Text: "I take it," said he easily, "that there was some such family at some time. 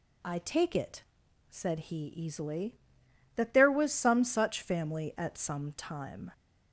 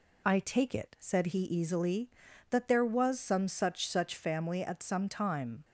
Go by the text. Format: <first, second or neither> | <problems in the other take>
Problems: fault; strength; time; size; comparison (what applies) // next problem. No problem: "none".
first | says "such" twice; at 3.8 s